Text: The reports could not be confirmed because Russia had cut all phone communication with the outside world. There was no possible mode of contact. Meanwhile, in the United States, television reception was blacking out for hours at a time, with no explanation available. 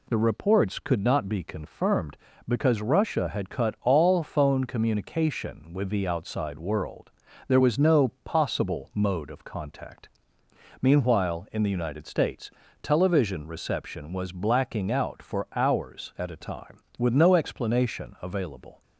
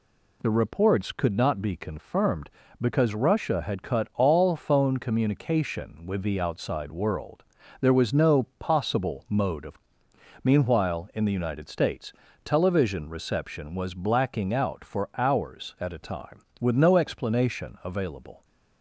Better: first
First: none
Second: skips "contact"; at 10.0 s

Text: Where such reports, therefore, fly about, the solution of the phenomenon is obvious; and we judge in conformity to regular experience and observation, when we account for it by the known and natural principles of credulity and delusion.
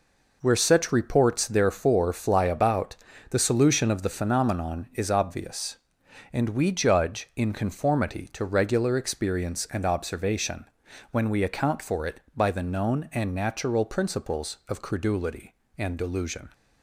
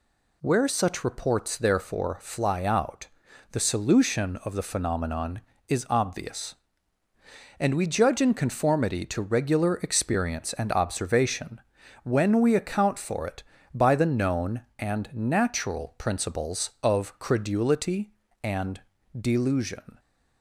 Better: first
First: none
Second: says "out" for "about"; at 2.6 s // pauses between "and" and "delusion"; slight; at 18.8 s; 0.34 s long

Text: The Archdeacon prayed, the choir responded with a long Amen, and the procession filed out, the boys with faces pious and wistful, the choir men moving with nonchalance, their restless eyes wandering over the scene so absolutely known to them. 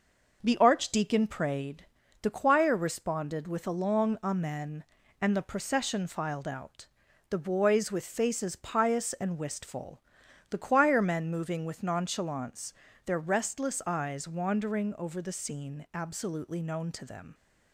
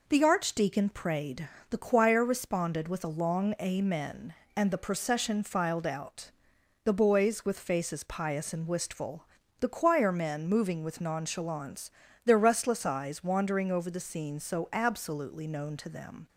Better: second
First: skips "so"; at 15.8 s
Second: none

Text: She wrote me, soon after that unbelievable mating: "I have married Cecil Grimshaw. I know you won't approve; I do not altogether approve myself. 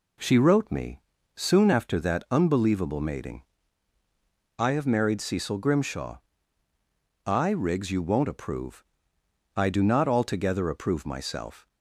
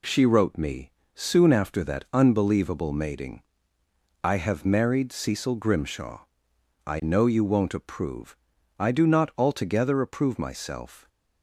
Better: second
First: says "riggs" for "know"; at 7.5 s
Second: none

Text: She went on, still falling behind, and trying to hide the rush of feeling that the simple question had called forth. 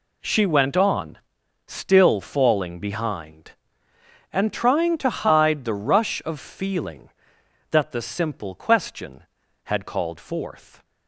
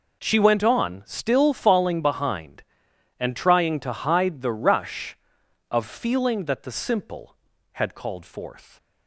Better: first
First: none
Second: skips "question"; at 7.5 s

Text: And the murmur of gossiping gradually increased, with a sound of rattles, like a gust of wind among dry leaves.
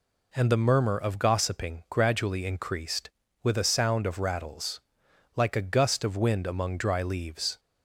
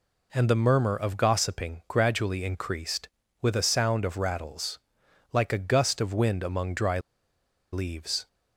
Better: first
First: none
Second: pauses between "dry" and "leaves"; noticeable; at 6.9 s; 0.72 s long

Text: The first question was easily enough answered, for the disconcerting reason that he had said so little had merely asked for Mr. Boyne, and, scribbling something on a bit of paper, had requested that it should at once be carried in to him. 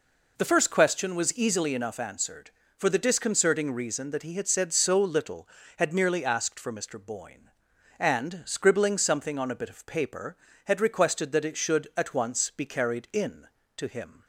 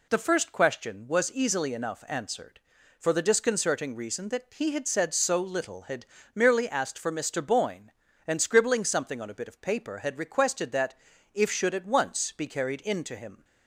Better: first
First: none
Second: pauses between "had" and "merely"; slight; at 6.0 s; 0.28 s long // says "if" for "it"; at 11.3 s

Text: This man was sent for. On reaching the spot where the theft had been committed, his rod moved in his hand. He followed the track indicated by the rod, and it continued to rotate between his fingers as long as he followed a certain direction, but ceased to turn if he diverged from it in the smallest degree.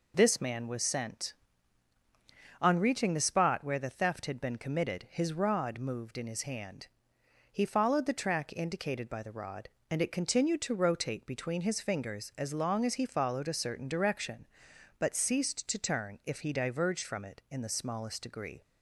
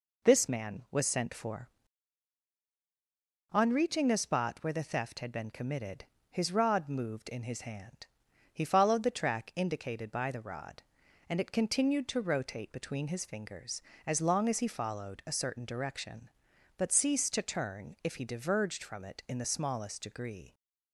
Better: second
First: skips "for"; at 1.9 s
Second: none

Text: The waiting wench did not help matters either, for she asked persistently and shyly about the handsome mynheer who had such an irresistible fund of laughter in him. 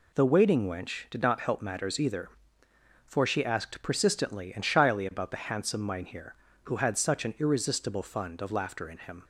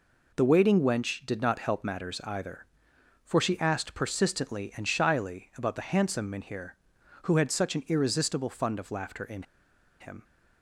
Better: first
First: none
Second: pauses between "in" and "him"; noticeable; at 9.4 s; 0.57 s long

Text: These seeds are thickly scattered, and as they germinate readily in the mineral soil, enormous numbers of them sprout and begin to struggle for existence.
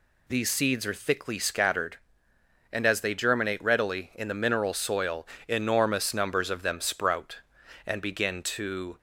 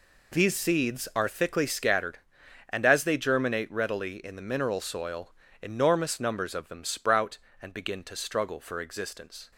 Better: second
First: stops before "struggle for existence"; at 8.9 s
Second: none

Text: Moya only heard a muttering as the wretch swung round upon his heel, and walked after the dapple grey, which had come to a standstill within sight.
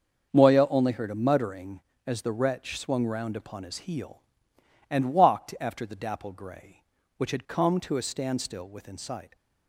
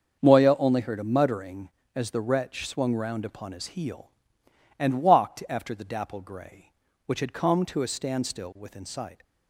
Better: neither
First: starts louder than the rest; until 1.3 s; 6.5 dB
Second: starts louder than the rest; until 1.2 s; 6.5 dB

